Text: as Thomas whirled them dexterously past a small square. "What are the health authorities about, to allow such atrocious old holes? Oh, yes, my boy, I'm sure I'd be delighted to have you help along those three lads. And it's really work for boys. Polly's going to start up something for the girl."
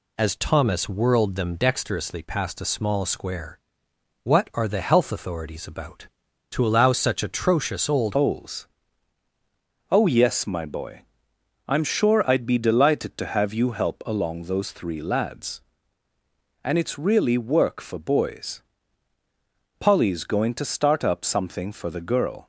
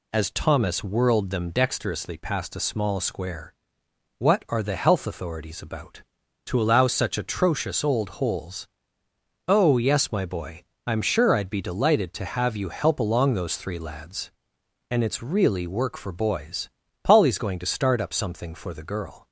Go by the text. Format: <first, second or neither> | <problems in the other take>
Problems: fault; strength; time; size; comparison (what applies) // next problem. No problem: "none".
second | changes voice at "holes"; from 8.1 s on; 14.3 s long